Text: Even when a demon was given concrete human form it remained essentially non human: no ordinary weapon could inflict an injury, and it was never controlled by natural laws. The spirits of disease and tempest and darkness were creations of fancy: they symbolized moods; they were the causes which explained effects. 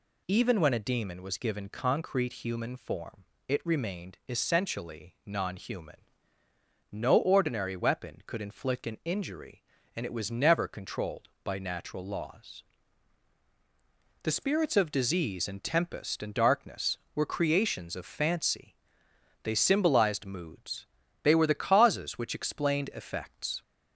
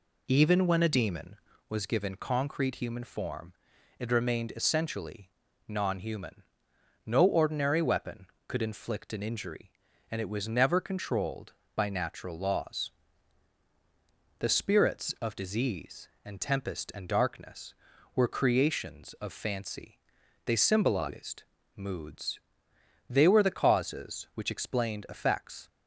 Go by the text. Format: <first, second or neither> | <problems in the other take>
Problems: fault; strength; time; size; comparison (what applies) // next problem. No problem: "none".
first | starts louder than the rest; slight; until 1.7 s; 3 dB // pauses between "form" and "it"; at 3.5 s; 0.44 s long; slight in the first // pauses between "essentially" and "non"; slight; at 5.3 s; 0.34 s long // pauses between "symbolized" and "moods"; slight; at 21.4 s; 0.32 s long